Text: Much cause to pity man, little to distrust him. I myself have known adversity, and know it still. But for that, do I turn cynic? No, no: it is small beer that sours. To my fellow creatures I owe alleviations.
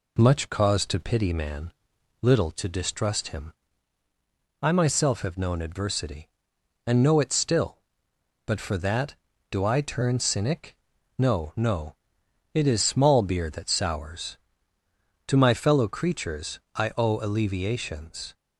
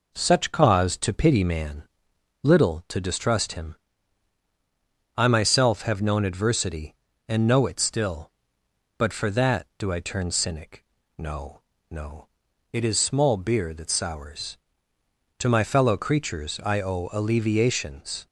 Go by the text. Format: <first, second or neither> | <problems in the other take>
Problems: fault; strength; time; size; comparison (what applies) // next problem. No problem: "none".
first | says "Such" for "Much"; at 0.1 s